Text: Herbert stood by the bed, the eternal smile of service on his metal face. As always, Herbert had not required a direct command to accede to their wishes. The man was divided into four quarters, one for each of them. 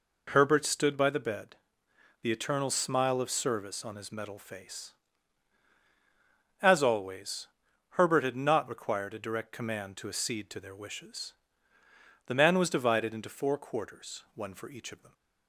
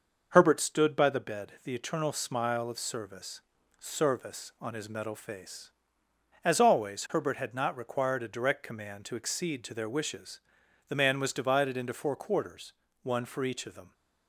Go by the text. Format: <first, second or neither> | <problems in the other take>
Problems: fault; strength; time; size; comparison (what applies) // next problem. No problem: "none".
first | starts louder than the rest; until 1.3 s; 6 dB // says "service" twice; at 3.7 s